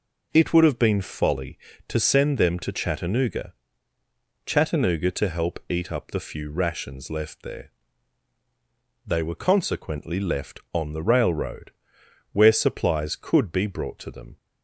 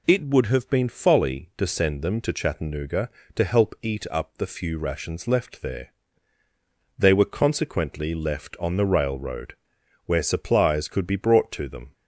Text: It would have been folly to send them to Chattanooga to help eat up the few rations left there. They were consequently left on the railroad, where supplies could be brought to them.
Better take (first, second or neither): second